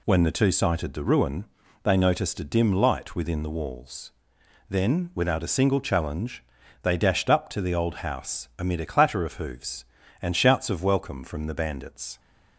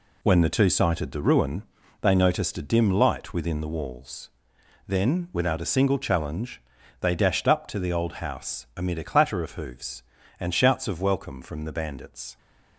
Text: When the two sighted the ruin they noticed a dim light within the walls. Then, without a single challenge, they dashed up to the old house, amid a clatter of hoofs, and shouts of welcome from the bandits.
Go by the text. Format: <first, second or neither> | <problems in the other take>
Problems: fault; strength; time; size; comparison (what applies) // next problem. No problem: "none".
first | gets quieter; strong; throughout; 8 dB // pauses between "ruin" and "they"; at 1.6 s; 0.38 s long; also in the first